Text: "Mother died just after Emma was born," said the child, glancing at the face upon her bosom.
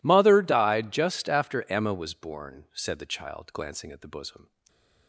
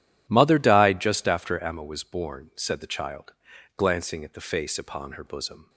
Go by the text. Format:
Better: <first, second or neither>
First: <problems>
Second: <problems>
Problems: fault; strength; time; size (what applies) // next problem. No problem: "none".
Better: second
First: skips "face upon her"; at 4.0 s // stays silent after the last word; slight; from 4.4 s on; 0.6 s long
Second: none